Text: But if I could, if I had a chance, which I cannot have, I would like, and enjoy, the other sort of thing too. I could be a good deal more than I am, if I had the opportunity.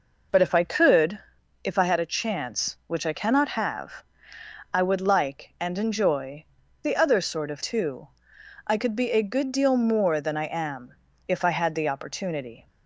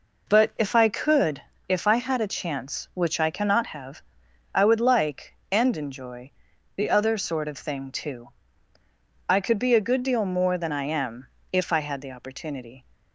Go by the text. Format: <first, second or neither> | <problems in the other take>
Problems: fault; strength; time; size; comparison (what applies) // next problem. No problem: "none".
second | skips "thing"; at 7.6 s